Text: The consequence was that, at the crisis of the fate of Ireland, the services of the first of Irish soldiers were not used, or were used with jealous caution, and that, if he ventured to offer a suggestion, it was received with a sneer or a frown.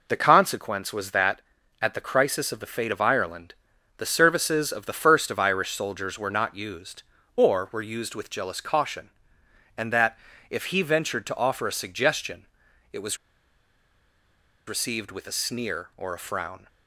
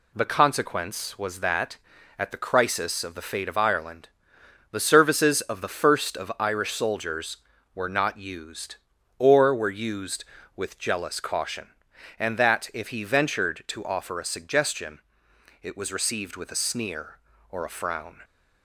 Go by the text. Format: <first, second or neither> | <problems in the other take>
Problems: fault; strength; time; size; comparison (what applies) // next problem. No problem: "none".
second | pauses between "was" and "received"; strong; at 13.1 s; 1.5 s long